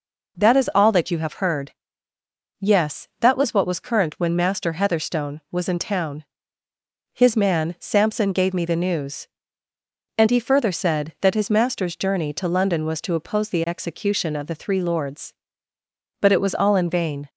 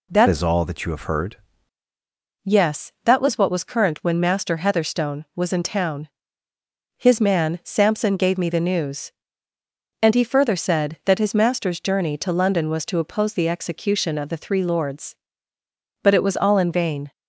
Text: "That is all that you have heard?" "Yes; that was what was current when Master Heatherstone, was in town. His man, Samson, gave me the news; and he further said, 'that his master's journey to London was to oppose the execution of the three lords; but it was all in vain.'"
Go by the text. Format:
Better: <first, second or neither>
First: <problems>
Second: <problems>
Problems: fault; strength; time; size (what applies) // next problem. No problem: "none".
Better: first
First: none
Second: changes voice from "is" to "heard"; from 0.2 to 1.3 s; 1.1 s long